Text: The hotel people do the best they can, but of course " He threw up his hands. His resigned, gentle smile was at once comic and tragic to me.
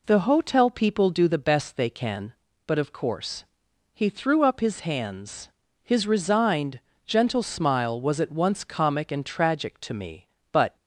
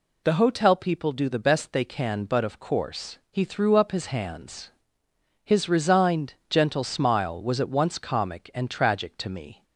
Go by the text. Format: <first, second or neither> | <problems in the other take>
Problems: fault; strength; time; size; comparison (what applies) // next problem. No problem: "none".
second | goes on to say "But"; slight; from 10.5 s on; 0.24 s long